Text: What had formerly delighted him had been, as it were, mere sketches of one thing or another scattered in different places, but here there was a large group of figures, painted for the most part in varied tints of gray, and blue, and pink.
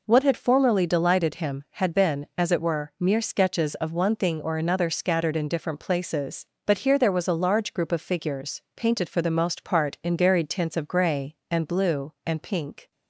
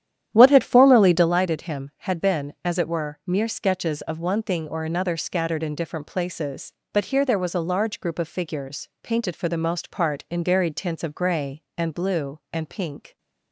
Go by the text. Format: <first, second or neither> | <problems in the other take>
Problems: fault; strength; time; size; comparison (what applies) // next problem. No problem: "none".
first | starts louder than the rest; strong; until 1.3 s; 10.5 dB